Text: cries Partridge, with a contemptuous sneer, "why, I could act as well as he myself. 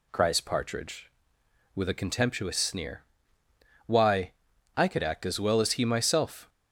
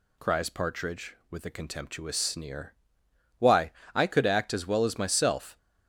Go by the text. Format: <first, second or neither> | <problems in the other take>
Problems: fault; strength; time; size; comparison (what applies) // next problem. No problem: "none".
first | skips "he"; at 4.9 s